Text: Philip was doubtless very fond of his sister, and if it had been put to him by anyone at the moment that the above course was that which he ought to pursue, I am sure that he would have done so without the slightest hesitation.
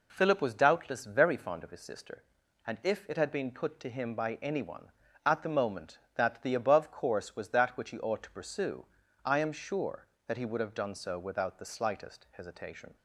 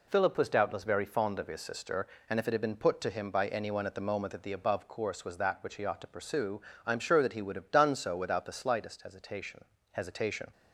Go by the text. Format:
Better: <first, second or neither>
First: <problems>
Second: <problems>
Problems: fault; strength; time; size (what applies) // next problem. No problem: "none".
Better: first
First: none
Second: says "hesitation" twice; at 9.9 s